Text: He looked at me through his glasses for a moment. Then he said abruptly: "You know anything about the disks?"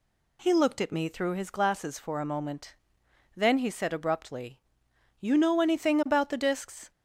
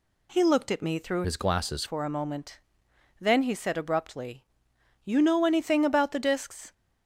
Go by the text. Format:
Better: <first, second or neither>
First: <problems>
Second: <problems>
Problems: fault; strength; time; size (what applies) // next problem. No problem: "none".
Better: first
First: none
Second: changes voice from "his" to "glasses"; from 1.2 to 1.8 s; 0.6 s long